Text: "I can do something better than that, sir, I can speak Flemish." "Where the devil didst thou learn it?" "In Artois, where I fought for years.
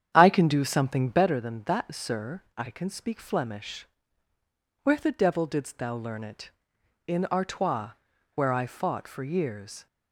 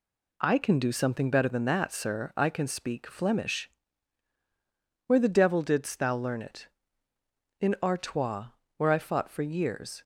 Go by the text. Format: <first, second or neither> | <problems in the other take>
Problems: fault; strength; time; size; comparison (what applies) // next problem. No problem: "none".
second | starts louder than the rest; strong; until 1.3 s; 9 dB